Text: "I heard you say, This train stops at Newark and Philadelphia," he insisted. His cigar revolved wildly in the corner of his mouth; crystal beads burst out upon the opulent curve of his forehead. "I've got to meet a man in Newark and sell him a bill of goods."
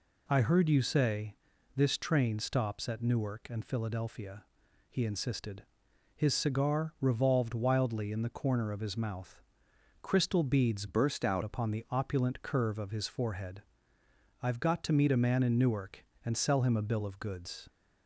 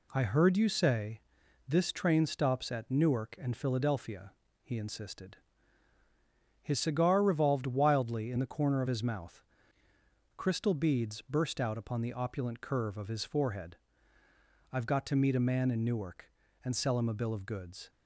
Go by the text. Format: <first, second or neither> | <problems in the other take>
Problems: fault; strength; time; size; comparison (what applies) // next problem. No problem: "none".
second | changes voice from "burst" to "out"; from 10.8 to 11.4 s; 0.6 s long